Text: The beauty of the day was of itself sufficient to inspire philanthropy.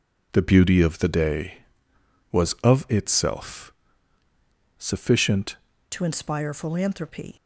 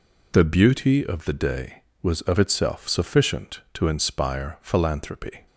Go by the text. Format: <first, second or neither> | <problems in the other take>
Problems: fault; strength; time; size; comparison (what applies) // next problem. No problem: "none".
second | pauses between "itself" and "sufficient"; at 3.7 s; 1.0 s long // changes voice at "to"; from 5.9 s on; 1.4 s long